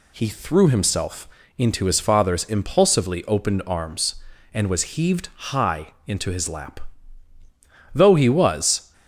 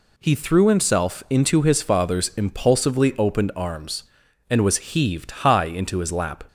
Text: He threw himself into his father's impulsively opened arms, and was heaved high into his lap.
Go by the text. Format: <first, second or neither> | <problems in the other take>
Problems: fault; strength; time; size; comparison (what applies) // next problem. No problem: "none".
second | pauses between "himself" and "into"; slight; at 1.2 s; 0.32 s long // pauses between "high" and "into"; slight; at 5.8 s; 0.18 s long // goes on to say "Though he was"; noticeable; from 7.9 s on; 1.0 s long